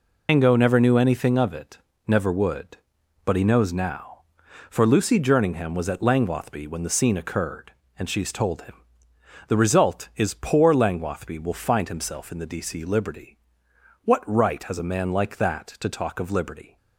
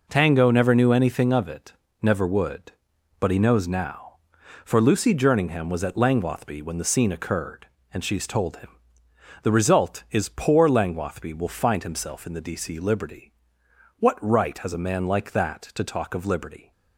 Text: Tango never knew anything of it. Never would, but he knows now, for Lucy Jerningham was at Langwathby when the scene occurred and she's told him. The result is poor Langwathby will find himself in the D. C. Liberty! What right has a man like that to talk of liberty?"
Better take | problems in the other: second | loses the start of "Tango"; at 0.2 s; 145 ms

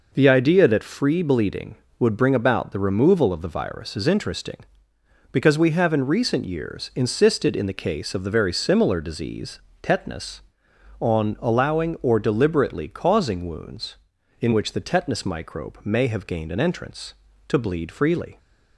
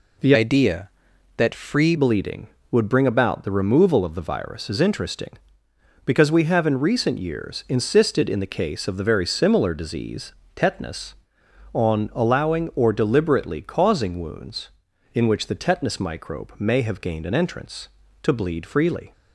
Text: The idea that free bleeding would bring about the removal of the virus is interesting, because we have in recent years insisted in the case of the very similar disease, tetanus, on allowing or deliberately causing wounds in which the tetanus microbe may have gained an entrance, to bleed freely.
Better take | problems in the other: first | changes voice from "idea" to "free"; from 0.3 to 1.9 s; 1.6 s long

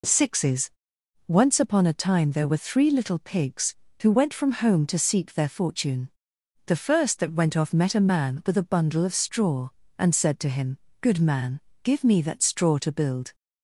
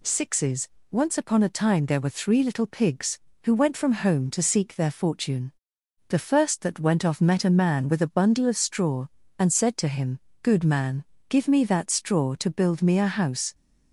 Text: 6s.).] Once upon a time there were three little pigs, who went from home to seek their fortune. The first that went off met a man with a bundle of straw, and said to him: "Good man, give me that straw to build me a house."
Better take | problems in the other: second | stops before "me a house"; at 13.3 s

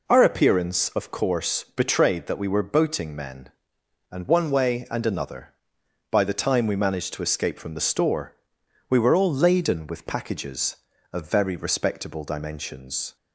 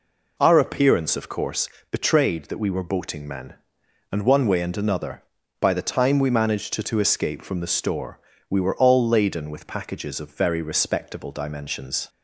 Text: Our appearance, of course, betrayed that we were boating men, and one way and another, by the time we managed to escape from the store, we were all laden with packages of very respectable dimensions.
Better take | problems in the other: first | says "to" twice; at 6.8 s

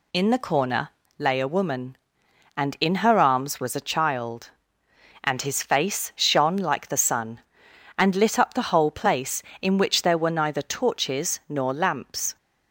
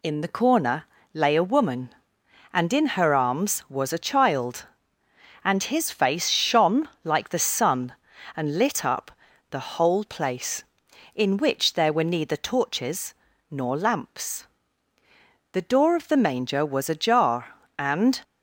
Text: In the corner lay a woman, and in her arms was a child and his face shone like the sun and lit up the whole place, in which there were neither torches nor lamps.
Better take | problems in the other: first | pauses between "corner" and "lay"; slight; at 0.8 s; 0.28 s long; slight in the first // pauses between "shone" and "like"; slight; at 6.8 s; 0.16 s long // pauses between "up" and "the"; at 9.1 s; 0.38 s long // pauses between "torches" and "nor"; slight; at 13.1 s; 0.34 s long // goes on to say "The door of the manger was ajar and"; strong; from 15.5 s on; 2.6 s long

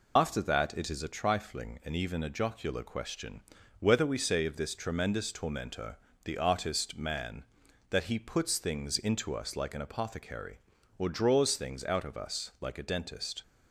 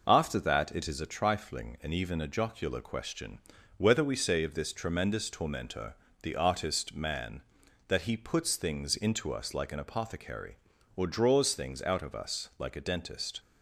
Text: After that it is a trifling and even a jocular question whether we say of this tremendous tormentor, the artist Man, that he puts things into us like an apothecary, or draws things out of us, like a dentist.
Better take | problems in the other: second | loses the start of "After"; at 0.1 s; 75 ms // pauses between "question" and "whether"; at 3.3 s; 0.40 s long; also in the second

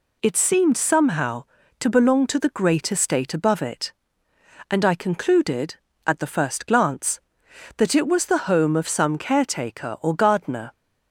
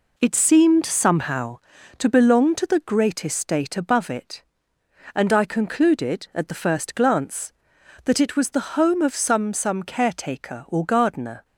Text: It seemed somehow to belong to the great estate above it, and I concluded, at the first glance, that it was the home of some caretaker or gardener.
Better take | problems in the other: first | says "some" twice; at 9.5 s

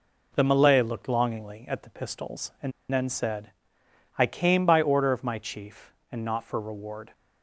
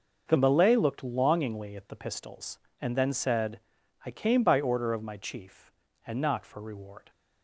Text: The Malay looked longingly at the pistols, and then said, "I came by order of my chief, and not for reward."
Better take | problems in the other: second | pauses between "and" and "then"; slight; at 2.7 s; 0.20 s long

